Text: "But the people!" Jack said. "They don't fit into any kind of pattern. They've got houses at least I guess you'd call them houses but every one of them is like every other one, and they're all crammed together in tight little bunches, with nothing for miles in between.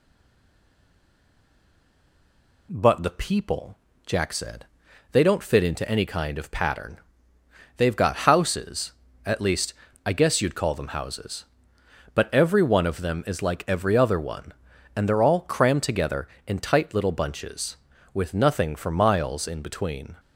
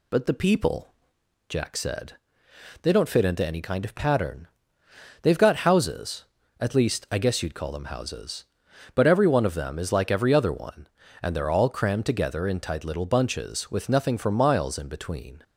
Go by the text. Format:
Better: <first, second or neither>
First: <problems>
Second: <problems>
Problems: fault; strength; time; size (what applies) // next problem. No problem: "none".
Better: second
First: stays silent before the first word; strong; until 2.6 s; 2.6 s long // pauses between "least" and "I"; slight; at 9.7 s; 0.32 s long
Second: none